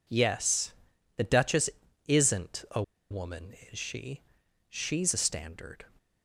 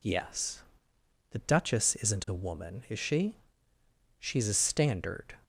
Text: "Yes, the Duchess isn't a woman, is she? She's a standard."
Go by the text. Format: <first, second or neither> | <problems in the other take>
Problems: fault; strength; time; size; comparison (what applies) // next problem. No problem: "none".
second | pauses between "Duchess" and "isn't"; at 1.6 s; 0.40 s long // pauses between "a" and "woman"; slight; at 2.8 s; 0.28 s long